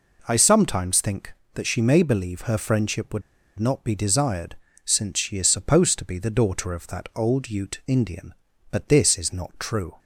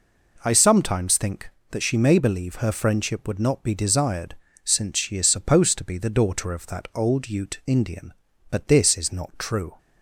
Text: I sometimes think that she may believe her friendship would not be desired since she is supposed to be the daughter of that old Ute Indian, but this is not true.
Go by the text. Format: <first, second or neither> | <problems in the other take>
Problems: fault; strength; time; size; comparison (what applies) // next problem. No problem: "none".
second | pauses between "would" and "not"; at 3.2 s; 0.37 s long // pauses between "desired" and "since"; slight; at 4.5 s; 0.30 s long; slight in the second